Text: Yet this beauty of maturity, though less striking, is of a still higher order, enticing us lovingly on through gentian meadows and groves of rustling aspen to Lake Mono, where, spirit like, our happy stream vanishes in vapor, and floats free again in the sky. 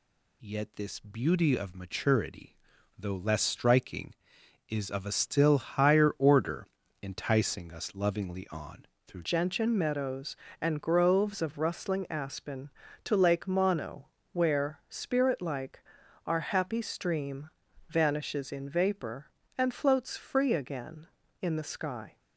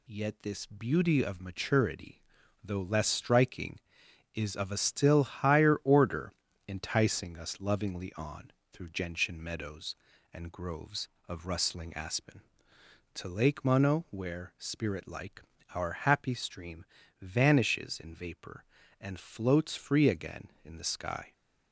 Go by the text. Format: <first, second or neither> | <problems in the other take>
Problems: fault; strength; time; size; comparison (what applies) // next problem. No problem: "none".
second | pauses between "on" and "through"; slight; at 8.8 s; 0.20 s long; slight in the second // changes voice at "gentian"; from 9.2 s on; 12.9 s long // pauses between "stream" and "vanishes"; at 17.4 s; 0.40 s long; slight in the second